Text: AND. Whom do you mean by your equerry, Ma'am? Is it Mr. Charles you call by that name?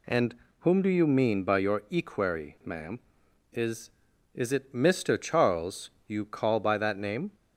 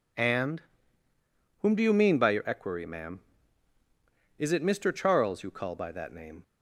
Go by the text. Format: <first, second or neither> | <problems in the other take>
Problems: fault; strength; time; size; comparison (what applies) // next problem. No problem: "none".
second | says "Is" twice; at 4.3 s // pauses between "Charles" and "you"; slight; at 5.9 s; 0.16 s long